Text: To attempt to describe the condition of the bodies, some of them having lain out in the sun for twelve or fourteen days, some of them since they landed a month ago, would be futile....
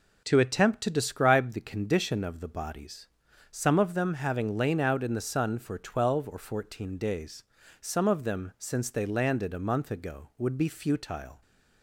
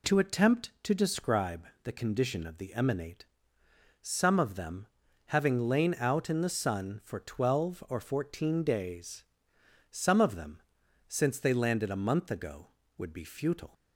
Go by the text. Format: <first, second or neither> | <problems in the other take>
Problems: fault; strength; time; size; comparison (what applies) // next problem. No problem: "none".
first | pauses between "describe" and "the"; slight; at 1.6 s; 0.18 s long // says "emanate" for "bodies"; at 2.7 s // pauses between "them" and "having"; at 4.8 s; 0.42 s long // pauses between "them" and "since"; noticeable; at 10.6 s; 0.46 s long